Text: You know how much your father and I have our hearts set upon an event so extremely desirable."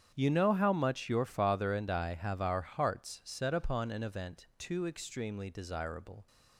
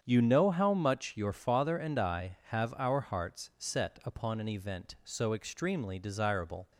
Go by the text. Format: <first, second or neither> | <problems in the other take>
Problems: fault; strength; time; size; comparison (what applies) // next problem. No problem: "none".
second | starts louder than the rest; strong; until 1.1 s; 8.5 dB; strong in the second // says "too" for "so"; at 4.5 s